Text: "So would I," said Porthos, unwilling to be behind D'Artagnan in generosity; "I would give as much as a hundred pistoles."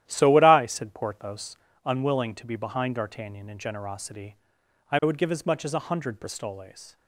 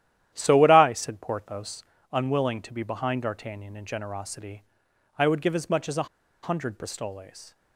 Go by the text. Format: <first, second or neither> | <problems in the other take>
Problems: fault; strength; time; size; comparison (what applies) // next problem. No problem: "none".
first | starts louder than the rest; strong; until 1.3 s; 11.5 dB; strong in the first // pauses between "a" and "hundred"; slight; at 6.0 s; 0.36 s long